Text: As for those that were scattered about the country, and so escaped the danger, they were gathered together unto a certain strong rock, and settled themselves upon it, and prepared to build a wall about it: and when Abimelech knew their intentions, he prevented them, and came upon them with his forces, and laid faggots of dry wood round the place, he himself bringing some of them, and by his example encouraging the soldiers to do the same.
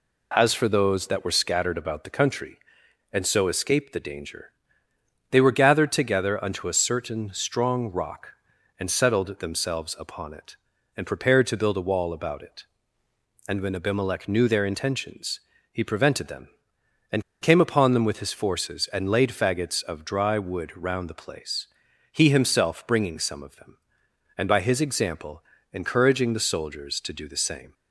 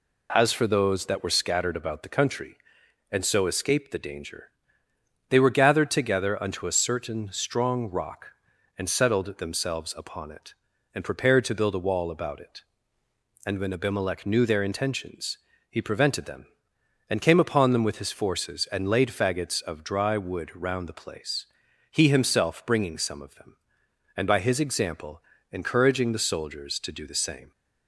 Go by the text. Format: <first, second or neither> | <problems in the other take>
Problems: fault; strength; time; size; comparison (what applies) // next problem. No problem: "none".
second | pauses between "and" and "came"; slight; at 17.2 s; 0.19 s long // pauses between "example" and "encouraging"; slight; at 25.4 s; 0.30 s long; slight in the second